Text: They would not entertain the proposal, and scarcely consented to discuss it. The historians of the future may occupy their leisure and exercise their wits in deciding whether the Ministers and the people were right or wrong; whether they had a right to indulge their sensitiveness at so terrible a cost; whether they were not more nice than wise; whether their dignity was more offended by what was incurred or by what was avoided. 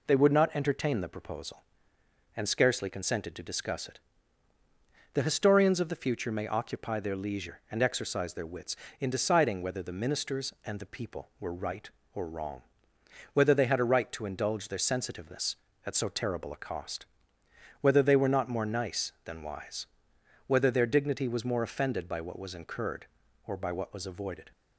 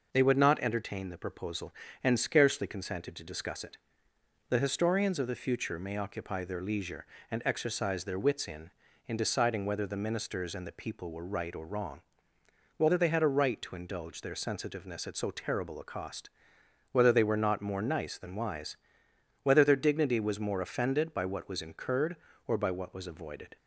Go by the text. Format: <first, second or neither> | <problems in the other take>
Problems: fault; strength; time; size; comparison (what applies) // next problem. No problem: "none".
first | says "in" twice; at 9.0 s